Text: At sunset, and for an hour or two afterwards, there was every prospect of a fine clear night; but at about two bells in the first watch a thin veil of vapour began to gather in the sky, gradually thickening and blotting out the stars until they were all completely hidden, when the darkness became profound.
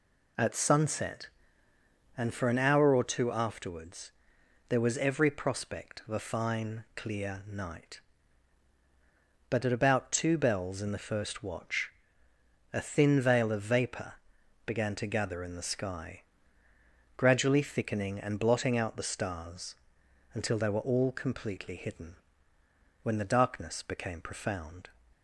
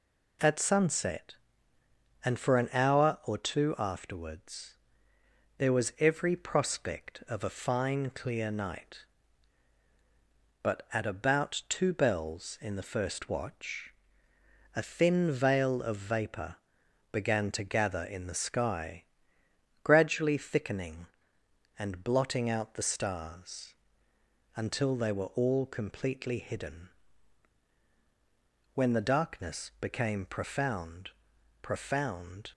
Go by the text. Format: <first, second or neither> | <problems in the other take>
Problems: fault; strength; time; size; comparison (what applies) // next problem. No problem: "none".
first | pauses between "watch" and "a"; noticeable; at 13.9 s; 0.84 s long; noticeable in the first // pauses between "vapour" and "began"; noticeable; at 16.5 s; 0.56 s long; noticeable in the first // pauses between "stars" and "until"; noticeable; at 23.7 s; 0.82 s long; noticeable in the first // says "profound" twice; at 31.6 s